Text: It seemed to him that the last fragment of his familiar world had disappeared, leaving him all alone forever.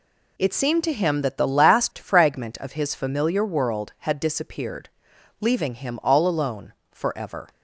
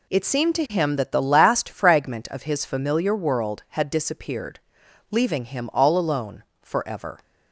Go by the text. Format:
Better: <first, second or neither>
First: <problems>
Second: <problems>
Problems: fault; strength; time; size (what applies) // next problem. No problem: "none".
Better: neither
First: pauses between "alone" and "forever"; slight; at 6.7 s; 0.18 s long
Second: pauses between "alone" and "forever"; slight; at 6.4 s; 0.18 s long